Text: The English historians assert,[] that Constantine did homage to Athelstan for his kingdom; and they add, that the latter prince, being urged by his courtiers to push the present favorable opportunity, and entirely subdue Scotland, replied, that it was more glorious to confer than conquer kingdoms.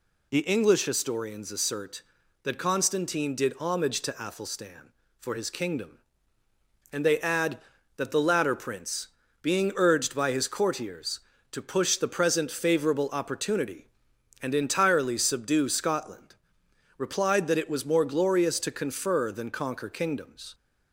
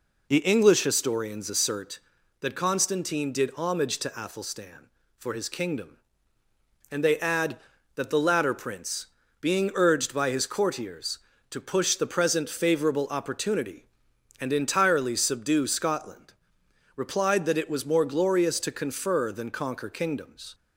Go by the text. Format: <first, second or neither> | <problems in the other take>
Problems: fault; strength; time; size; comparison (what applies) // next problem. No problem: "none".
first | starts louder than the rest; until 2.0 s; 3.5 dB